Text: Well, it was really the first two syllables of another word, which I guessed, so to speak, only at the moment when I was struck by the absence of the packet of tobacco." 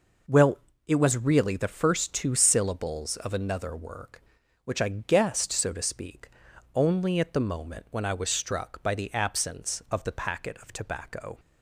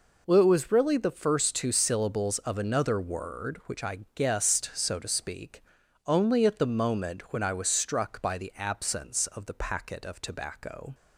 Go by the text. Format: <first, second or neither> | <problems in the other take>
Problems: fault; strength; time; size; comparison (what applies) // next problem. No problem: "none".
second | says "work" for "word"; at 3.7 s